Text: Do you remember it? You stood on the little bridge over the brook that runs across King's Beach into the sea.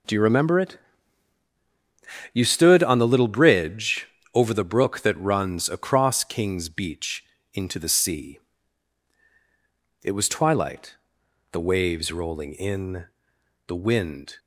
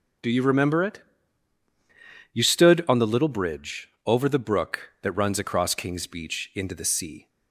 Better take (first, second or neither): second